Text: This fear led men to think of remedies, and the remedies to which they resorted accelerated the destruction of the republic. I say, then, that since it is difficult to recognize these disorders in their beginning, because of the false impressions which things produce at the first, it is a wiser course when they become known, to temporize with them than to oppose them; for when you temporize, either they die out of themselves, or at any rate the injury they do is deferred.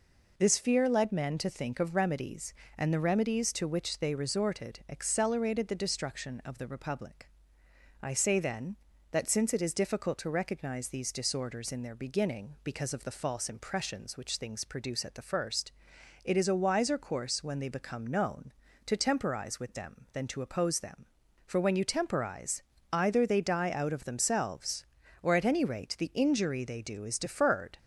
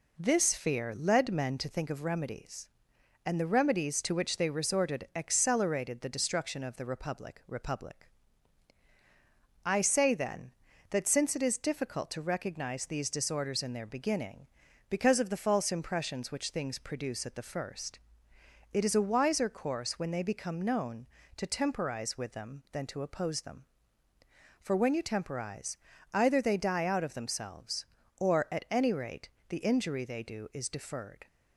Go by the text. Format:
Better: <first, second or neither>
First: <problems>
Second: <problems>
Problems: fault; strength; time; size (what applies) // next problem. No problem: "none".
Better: first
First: none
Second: says "republic" twice; at 7.4 s // pauses between "rate" and "the"; slight; at 29.2 s; 0.20 s long